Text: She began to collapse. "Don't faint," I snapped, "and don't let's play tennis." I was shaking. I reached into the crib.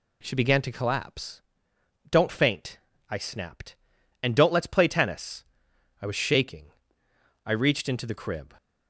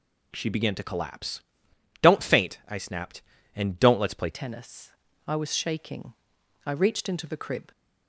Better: first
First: none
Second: changes voice at "tennis"; from 4.3 s on; 3.4 s long

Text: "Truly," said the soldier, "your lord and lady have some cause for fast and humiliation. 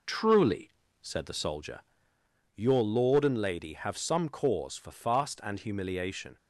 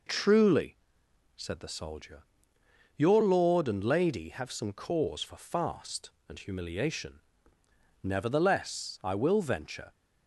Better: first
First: none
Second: goes on to say "Nevertheless I will venture"; strong; from 8.0 s on; 1.9 s long

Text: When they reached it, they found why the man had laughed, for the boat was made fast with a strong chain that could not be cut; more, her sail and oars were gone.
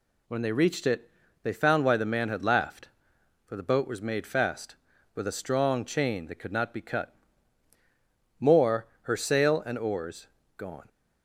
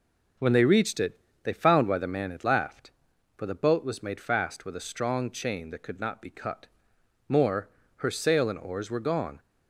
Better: second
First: skips "were"; at 10.4 s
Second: none

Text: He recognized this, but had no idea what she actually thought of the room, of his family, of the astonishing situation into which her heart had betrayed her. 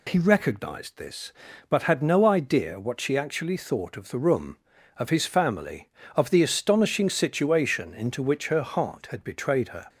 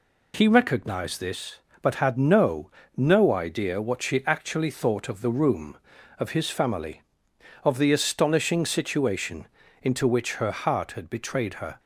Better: first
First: none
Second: says "no" twice; at 2.9 s // pauses between "situation" and "into"; slight; at 9.4 s; 0.34 s long

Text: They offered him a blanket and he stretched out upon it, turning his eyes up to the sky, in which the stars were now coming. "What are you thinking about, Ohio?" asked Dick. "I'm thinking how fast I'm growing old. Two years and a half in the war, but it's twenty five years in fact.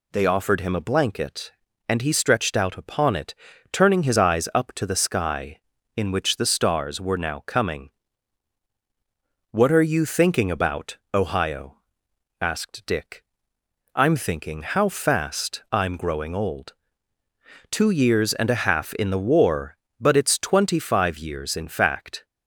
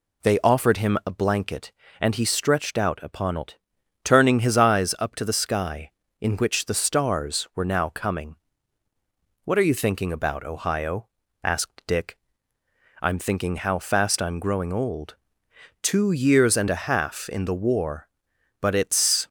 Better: first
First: none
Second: stops before "twenty five years in fact"; at 19.2 s

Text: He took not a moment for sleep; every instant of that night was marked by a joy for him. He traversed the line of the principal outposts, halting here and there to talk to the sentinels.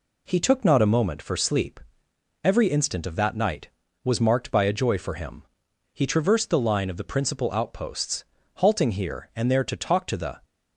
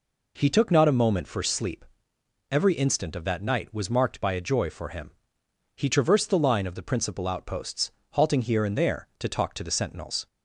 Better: second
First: stops before "sentinels"; at 10.4 s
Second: none

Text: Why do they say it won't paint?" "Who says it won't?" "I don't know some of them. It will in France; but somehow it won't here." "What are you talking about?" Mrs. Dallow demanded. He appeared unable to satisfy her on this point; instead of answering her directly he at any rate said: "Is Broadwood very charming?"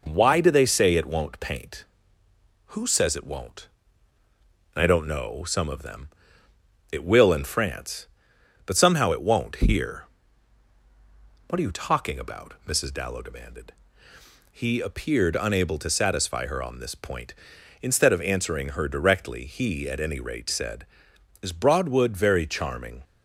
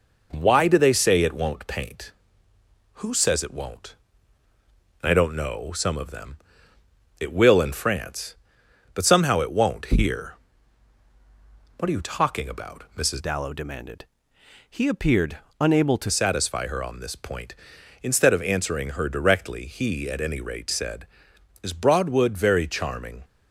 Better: first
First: none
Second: changes voice from "Dallow" to "to"; from 13.2 to 16.1 s; 2.9 s long // pauses between "appeared" and "unable"; slight; at 15.3 s; 0.22 s long

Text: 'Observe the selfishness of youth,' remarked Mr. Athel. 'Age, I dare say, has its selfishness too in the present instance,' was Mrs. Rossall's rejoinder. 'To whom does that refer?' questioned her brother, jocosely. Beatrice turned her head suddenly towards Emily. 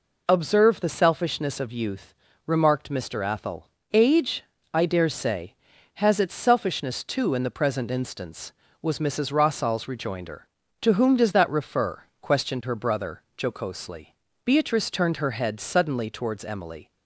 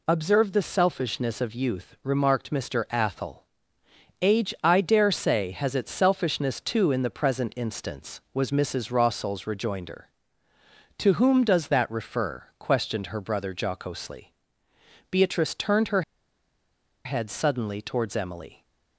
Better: first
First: none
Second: pauses between "her" and "head"; at 16.0 s; 1.0 s long

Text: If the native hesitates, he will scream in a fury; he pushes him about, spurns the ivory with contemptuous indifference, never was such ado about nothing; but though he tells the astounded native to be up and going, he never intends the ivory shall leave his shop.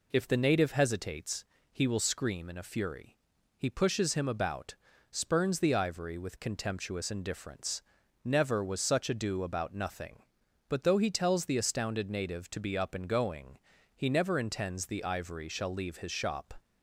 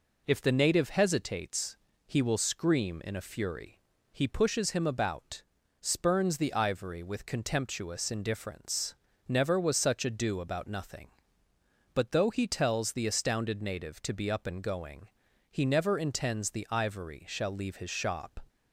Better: neither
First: none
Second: none

